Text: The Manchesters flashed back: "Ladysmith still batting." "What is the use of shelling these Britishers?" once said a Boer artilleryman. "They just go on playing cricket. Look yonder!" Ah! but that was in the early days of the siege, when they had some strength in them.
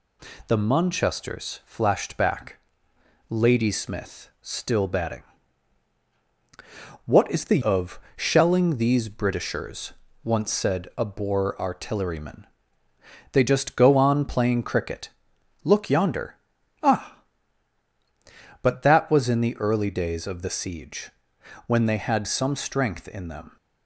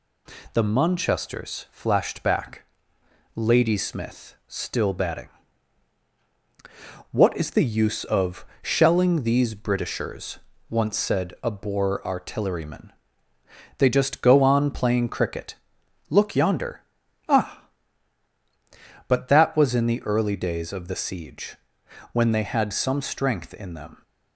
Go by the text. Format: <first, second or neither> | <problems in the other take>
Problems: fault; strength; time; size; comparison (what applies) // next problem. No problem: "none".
second | skips "use"; at 7.6 s // pauses between "of" and "shelling"; slight; at 8.0 s; 0.16 s long; slight in the second